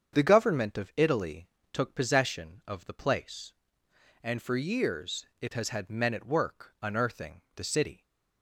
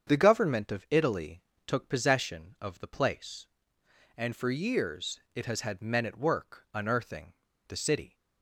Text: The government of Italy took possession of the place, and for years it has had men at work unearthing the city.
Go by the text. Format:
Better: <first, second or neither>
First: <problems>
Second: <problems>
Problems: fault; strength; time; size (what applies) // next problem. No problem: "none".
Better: first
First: starts louder than the rest; strong; until 1.1 s; 7.5 dB // pauses between "Italy" and "took"; slight; at 1.4 s; 0.24 s long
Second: starts louder than the rest; strong; until 1.1 s; 7.5 dB // pauses between "Italy" and "took"; slight; at 1.4 s; 0.24 s long // pauses between "unearthing" and "the"; slight; at 7.3 s; 0.34 s long